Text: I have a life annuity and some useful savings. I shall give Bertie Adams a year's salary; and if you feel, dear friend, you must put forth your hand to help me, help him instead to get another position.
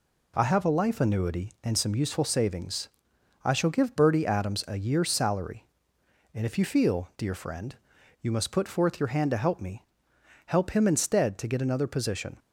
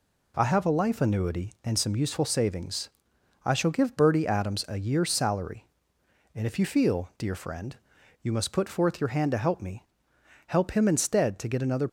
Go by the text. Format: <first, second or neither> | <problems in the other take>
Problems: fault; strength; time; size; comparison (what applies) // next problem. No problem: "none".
first | stops before "position"; at 11.8 s